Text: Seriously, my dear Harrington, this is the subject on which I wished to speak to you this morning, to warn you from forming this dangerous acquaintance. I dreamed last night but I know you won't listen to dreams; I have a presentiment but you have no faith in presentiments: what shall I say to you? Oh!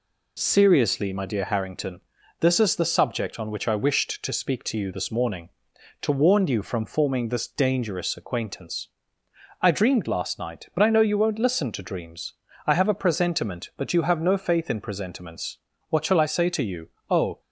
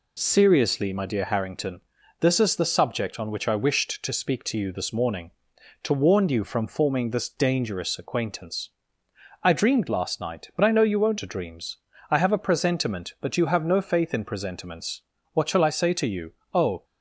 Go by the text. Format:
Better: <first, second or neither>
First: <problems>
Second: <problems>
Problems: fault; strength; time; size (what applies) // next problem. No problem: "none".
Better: first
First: none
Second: skips "listen"; at 11.1 s